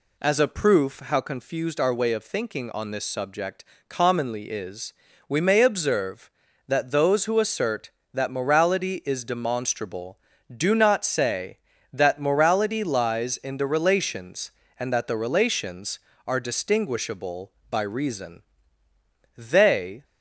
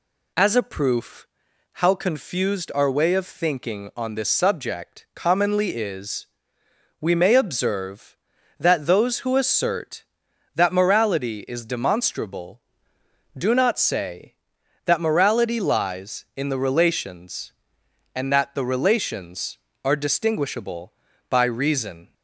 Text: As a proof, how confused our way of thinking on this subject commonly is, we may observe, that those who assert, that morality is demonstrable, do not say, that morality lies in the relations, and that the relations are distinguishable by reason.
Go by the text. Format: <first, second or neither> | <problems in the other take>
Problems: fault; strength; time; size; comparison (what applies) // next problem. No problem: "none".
second | pauses between "subject" and "commonly"; slight; at 3.6 s; 0.24 s long // goes on to say "They"; noticeable; from 19.3 s on; 0.68 s long